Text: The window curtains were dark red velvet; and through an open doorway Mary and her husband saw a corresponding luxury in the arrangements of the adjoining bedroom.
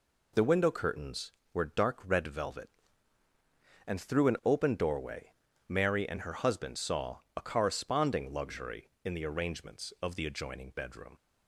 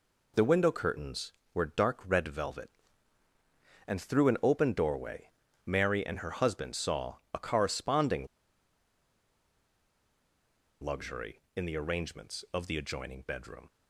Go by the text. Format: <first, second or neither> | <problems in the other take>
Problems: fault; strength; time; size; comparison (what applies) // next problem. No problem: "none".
first | pauses between "doorway" and "Mary"; slight; at 5.2 s; 0.36 s long; slight in the first // pauses between "corresponding" and "luxury"; strong; at 8.2 s; 2.5 s long